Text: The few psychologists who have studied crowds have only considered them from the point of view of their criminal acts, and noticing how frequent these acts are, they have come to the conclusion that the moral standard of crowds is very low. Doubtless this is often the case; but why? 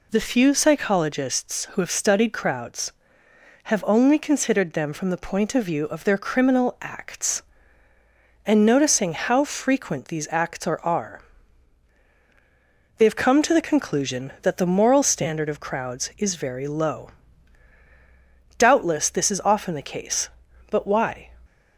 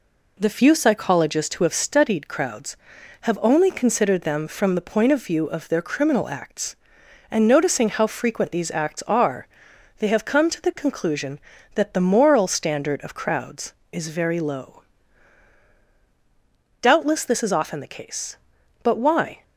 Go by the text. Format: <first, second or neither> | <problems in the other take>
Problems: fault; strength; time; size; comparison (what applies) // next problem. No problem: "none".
second | says "are" twice; at 10.8 s